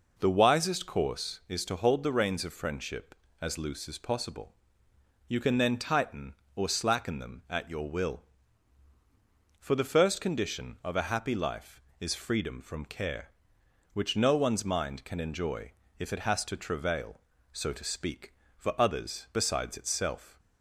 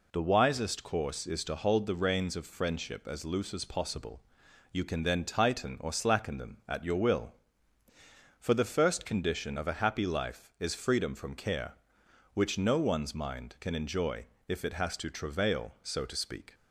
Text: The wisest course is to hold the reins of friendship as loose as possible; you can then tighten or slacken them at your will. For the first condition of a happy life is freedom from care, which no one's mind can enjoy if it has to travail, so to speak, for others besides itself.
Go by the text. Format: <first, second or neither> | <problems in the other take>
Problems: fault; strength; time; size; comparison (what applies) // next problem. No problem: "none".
first | pauses between "enjoy" and "if"; slight; at 14.2 s; 0.20 s long; slight in the first // stops before "for others besides itself"; at 16.5 s